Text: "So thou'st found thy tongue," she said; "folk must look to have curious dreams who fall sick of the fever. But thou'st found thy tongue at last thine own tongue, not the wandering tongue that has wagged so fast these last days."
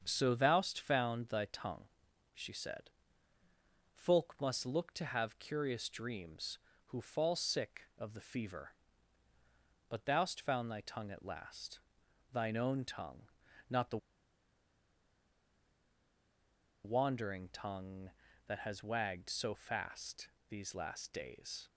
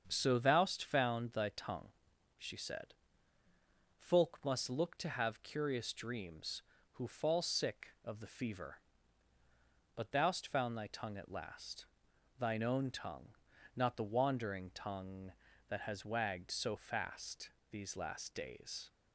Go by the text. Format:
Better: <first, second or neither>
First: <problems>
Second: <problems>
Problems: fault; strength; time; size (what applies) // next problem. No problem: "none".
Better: second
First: starts louder than the rest; strong; until 1.0 s; 7.5 dB // pauses between "last" and "thine"; noticeable; at 11.7 s; 0.54 s long // pauses between "the" and "wandering"; strong; at 13.9 s; 2.8 s long // pauses between "fast" and "these"; slight; at 20.2 s; 0.20 s long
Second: starts louder than the rest; strong; until 1.0 s; 7.5 dB // pauses between "last" and "thine"; noticeable; at 11.8 s; 0.54 s long // pauses between "fast" and "these"; slight; at 17.5 s; 0.20 s long